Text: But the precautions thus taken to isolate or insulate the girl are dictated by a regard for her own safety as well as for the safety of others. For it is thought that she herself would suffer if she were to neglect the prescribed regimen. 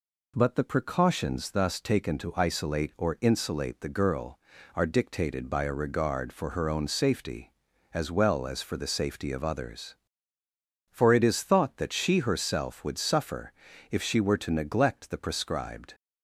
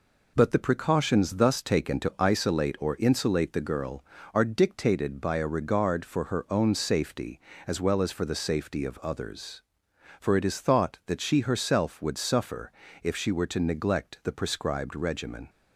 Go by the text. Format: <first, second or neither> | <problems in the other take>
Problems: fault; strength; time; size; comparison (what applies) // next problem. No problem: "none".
second | pauses between "suffer" and "if"; slight; at 13.5 s; 0.36 s long; slight in the second // stops before "regimen"; at 15.9 s